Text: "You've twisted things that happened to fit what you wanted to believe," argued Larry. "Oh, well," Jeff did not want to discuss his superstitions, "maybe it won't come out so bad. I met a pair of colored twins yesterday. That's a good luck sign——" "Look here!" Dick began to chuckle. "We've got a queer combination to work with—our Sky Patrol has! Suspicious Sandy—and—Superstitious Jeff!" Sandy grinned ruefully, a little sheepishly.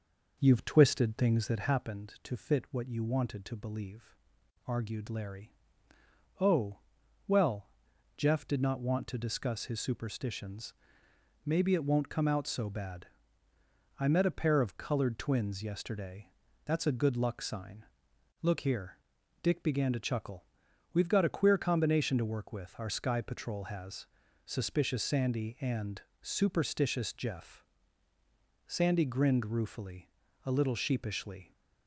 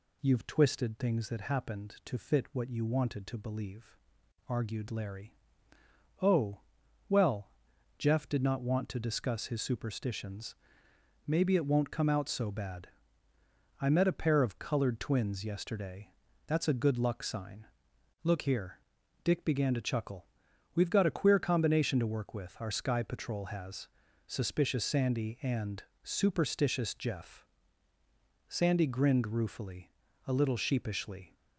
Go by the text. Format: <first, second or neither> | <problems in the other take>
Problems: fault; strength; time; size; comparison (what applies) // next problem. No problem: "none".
second | starts louder than the rest; noticeable; until 1.8 s; 5.5 dB